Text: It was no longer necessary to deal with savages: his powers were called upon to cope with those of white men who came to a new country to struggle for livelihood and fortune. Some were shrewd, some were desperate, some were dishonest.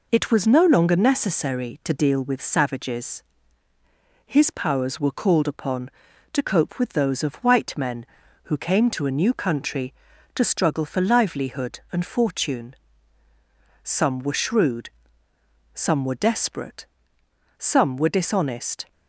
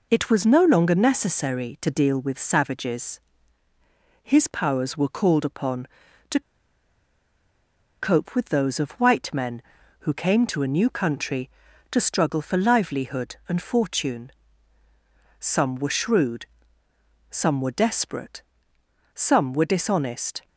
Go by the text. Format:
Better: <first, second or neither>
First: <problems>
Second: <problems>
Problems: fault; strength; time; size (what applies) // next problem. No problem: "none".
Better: first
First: none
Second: pauses between "to" and "cope"; strong; at 6.4 s; 1.6 s long